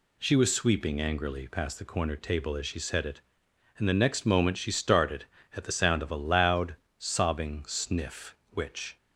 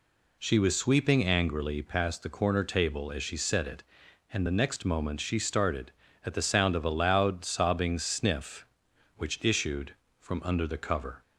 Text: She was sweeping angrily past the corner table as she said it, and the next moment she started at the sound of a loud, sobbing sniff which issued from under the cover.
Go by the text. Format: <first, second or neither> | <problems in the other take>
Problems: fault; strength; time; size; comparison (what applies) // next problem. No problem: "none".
second | stops before "issued from under the cover"; at 8.9 s